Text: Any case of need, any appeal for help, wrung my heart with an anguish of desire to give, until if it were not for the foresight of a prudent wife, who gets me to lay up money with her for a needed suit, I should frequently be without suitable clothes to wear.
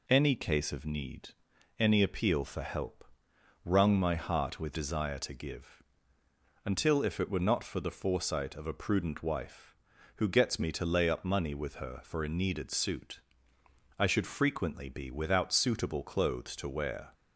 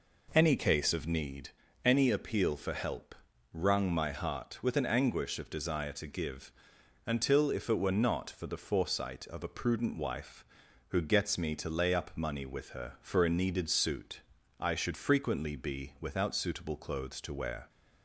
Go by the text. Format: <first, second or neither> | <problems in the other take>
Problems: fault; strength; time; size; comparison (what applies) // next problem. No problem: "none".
second | skips "an anguish of"; at 4.7 s